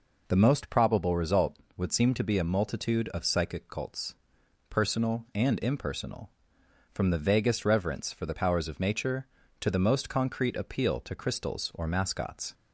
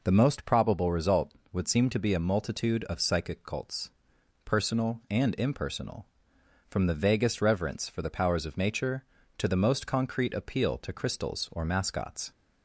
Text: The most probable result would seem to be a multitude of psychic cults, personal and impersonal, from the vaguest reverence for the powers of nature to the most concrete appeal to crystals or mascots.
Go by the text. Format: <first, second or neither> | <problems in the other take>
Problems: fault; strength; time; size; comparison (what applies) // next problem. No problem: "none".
neither | none